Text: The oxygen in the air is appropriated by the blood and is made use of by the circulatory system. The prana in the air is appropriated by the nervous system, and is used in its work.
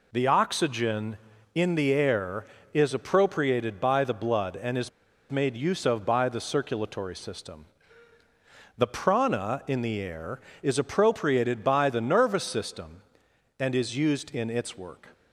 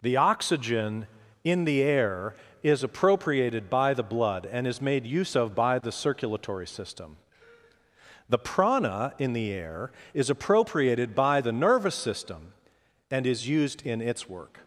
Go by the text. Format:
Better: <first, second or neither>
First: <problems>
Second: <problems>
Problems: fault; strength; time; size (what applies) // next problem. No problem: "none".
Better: second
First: pauses between "is" and "made"; at 4.8 s; 0.40 s long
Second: none